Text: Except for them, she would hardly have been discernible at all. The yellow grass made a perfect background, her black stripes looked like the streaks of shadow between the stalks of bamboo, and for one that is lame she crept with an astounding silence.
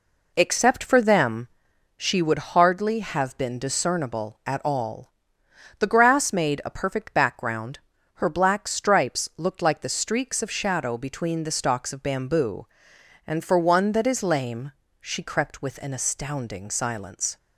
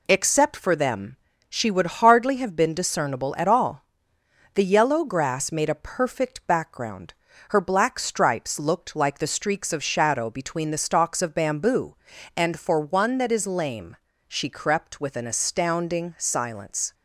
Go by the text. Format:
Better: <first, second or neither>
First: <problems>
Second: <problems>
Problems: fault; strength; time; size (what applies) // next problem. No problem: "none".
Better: second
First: skips "yellow"; at 5.8 s // pauses between "lame" and "she"; slight; at 14.7 s; 0.30 s long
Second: pauses between "lame" and "she"; slight; at 13.9 s; 0.28 s long